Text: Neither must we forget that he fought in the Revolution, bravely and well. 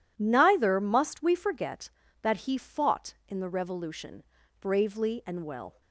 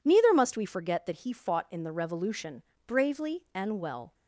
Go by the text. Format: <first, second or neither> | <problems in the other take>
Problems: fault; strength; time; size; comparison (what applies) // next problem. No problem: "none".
neither | none